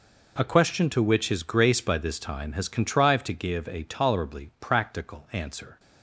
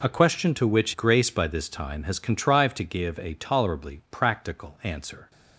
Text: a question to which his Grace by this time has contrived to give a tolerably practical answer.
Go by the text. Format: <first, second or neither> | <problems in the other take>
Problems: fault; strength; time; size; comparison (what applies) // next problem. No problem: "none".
first | skips "his"; at 0.9 s